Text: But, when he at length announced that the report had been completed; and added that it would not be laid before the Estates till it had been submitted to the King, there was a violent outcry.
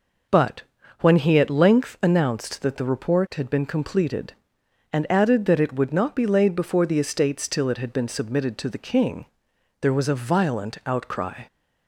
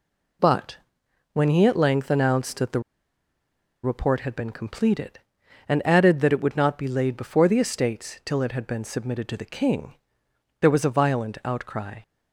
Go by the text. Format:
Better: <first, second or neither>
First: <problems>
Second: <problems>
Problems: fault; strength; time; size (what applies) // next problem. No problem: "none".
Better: first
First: none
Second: pauses between "the" and "report"; at 2.8 s; 1.0 s long